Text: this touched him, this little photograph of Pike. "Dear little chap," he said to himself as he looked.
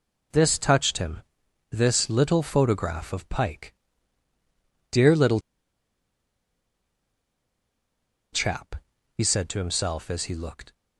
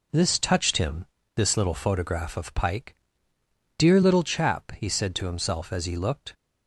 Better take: second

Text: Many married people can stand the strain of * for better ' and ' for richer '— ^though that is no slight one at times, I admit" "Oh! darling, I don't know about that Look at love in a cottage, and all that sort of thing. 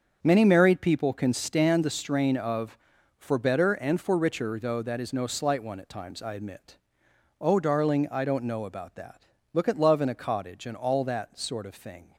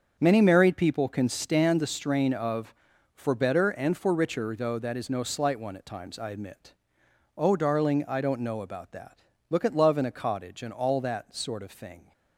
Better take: neither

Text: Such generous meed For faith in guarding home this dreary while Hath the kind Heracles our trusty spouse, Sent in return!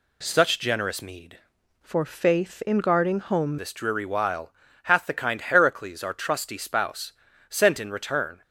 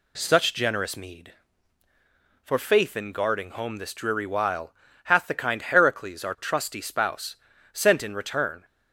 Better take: second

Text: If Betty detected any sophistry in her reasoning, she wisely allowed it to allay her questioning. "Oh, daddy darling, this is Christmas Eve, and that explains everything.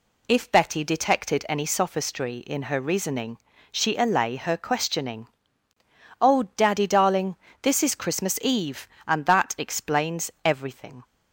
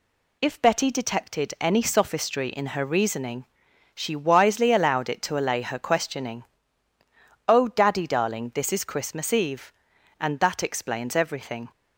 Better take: second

